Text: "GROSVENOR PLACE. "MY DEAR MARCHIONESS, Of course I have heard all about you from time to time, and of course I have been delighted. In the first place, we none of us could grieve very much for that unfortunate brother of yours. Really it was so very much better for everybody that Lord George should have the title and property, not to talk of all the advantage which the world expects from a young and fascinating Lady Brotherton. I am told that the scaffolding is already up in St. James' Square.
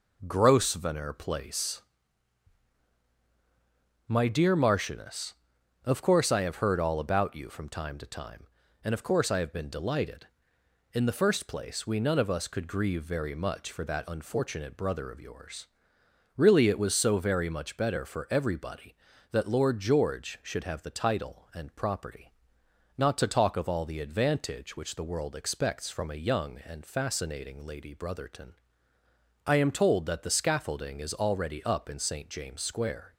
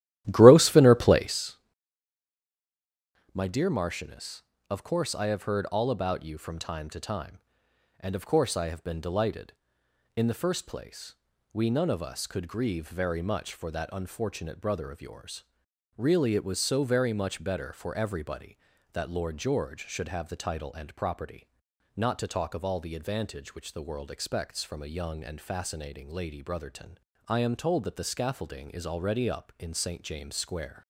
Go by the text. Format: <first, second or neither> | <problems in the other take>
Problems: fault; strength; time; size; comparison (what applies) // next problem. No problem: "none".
first | starts louder than the rest; strong; until 1.5 s; 14 dB